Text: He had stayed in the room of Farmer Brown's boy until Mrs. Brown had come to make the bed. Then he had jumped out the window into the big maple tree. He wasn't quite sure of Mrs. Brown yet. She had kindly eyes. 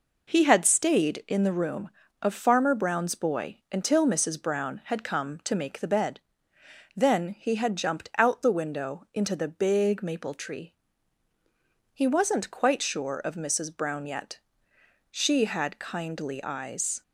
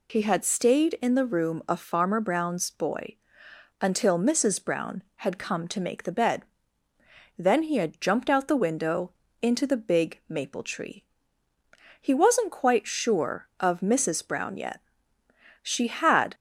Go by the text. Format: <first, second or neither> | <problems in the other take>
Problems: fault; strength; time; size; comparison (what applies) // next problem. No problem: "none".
first | pauses between "boy" and "until"; noticeable; at 3.1 s; 0.66 s long // pauses between "window" and "into"; slight; at 9.1 s; 0.28 s long // stops before "kindly eyes"; at 16.3 s